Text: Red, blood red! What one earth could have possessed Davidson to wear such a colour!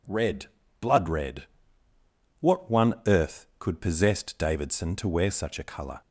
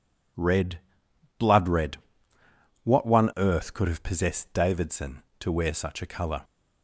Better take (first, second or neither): second